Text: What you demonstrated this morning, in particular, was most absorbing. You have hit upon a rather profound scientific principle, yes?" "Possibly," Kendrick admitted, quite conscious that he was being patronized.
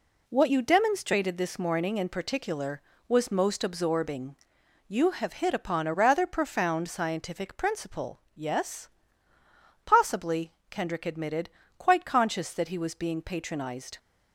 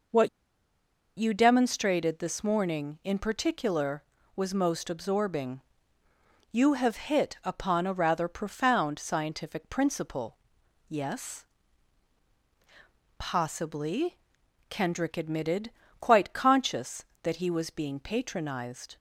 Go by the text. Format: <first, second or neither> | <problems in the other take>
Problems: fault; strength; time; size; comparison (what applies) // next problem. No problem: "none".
first | pauses between "What" and "you"; noticeable; at 0.2 s; 0.89 s long